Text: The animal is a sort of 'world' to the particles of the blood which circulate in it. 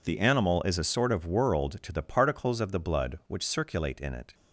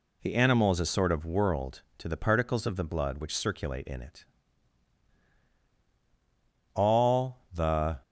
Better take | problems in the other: first | goes on to say "All the"; noticeable; from 6.7 s on; 1.2 s long

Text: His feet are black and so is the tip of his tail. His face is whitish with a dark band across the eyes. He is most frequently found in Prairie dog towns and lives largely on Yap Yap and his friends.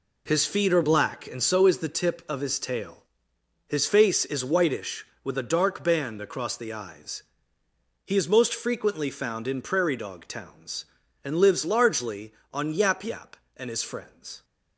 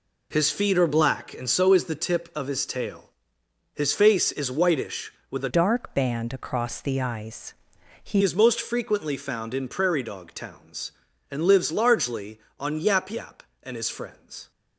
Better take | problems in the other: first | changes voice from "dark" to "He"; from 5.4 to 8.2 s; 2.8 s long

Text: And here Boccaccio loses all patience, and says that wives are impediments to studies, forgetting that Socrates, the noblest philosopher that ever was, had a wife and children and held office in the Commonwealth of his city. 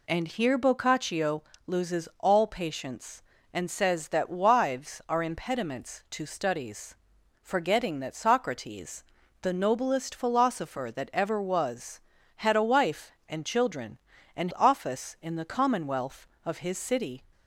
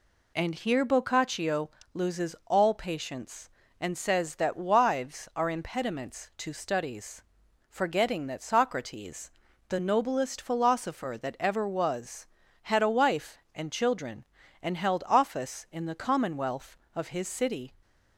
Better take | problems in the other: second | pauses between "Boccaccio" and "loses"; slight; at 1.4 s; 0.24 s long; slight in the second // skips "held"; at 14.5 s

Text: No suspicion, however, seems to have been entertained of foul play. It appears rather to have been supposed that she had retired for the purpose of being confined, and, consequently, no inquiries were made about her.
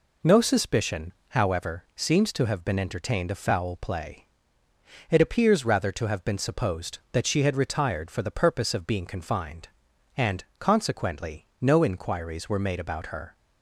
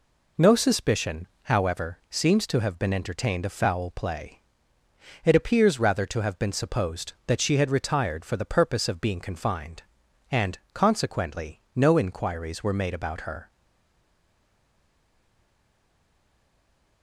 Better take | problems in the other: first | stays silent after the last word; strong; from 13.5 s on; 3.5 s long

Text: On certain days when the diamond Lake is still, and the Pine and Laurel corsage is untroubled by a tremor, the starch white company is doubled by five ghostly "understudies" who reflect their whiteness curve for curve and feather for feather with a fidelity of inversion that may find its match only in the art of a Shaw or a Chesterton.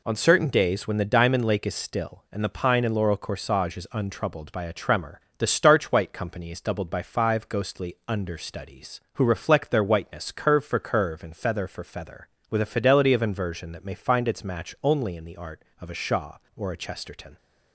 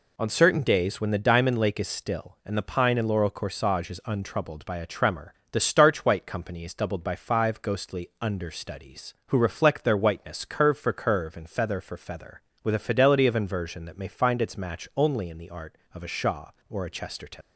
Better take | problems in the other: first | leaves "Chesterton" unfinished; at 17.4 s; 85 ms

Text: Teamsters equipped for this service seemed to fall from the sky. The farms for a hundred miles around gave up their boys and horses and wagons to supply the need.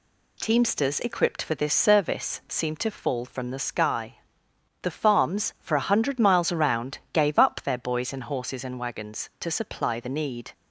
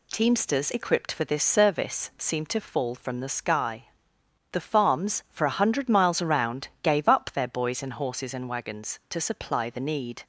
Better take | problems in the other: neither | none

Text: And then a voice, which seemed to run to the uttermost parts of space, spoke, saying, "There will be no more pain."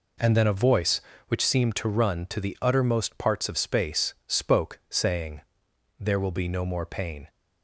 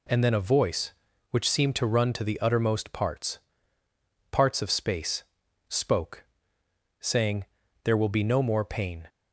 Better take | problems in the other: first | says "parts" twice; at 4.3 s

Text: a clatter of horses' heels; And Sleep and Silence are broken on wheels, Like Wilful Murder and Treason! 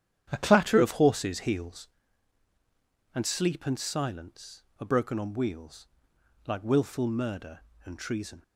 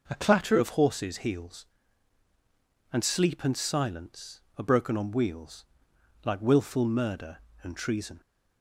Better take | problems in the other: second | starts louder than the rest; strong; until 2.0 s; 9.5 dB

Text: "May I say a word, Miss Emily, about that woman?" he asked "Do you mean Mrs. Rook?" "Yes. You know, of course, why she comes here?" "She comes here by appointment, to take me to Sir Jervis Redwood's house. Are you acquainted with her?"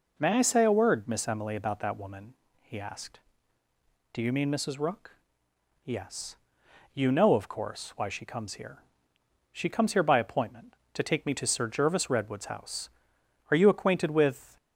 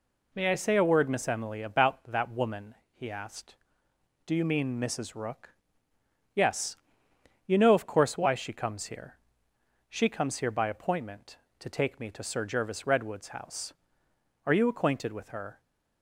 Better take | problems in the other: second | stops before "her"; at 14.5 s

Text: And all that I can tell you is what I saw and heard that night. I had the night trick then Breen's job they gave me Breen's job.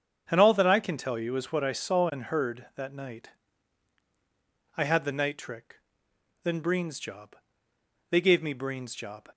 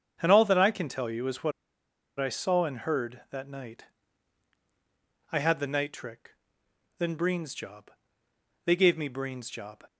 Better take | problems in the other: first | starts louder than the rest; strong; until 1.2 s; 7 dB; strong in the first // pauses between "what" and "I"; noticeable; at 1.5 s; 0.68 s long // pauses between "trick" and "then"; noticeable; at 6.3 s; 0.68 s long; noticeable in the first // pauses between "job" and "they"; noticeable; at 7.9 s; 0.74 s long; noticeable in the first

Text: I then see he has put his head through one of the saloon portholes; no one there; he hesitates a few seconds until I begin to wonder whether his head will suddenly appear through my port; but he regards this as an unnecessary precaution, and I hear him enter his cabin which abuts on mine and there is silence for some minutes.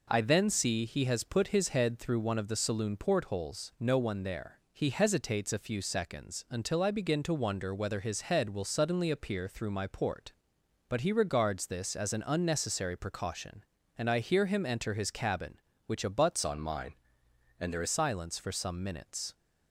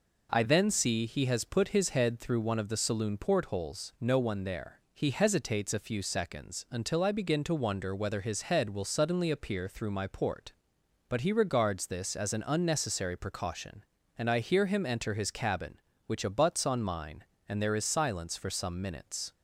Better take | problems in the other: second | changes voice from "on" to "is"; from 16.4 to 17.8 s; 1.4 s long

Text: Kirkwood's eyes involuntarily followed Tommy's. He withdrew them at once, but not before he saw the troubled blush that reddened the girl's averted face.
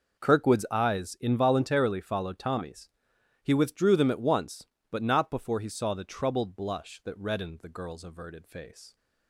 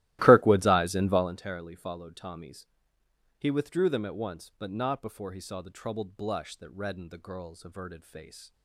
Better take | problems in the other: first | starts louder than the rest; strong; until 1.3 s; 16 dB

